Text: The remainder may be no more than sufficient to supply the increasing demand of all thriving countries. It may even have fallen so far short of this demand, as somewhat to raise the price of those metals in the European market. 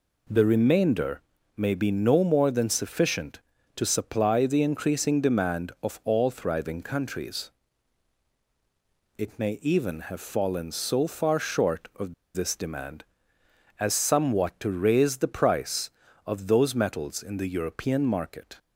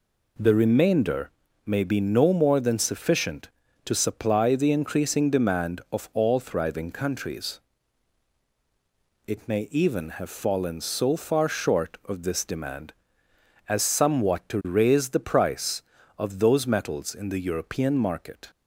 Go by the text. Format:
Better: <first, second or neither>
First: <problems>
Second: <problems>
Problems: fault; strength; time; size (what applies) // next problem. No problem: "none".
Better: second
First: pauses between "remainder" and "may"; slight; at 1.2 s; 0.34 s long // pauses between "of" and "this"; slight; at 12.1 s; 0.20 s long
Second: pauses between "remainder" and "may"; slight; at 1.3 s; 0.34 s long